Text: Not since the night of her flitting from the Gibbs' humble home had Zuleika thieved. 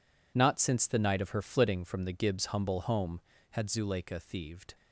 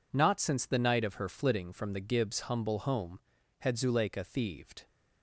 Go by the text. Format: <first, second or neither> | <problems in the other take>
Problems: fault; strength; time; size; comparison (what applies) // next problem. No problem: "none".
neither | none